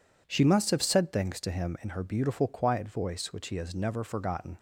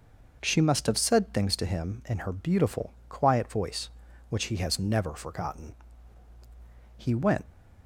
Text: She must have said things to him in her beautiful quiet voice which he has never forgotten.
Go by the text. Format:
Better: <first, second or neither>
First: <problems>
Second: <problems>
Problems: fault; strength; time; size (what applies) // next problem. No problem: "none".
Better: first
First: none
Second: pauses between "beautiful" and "quiet"; slight; at 2.9 s; 0.16 s long // goes on to say "He went"; slight; from 6.9 s on; 0.48 s long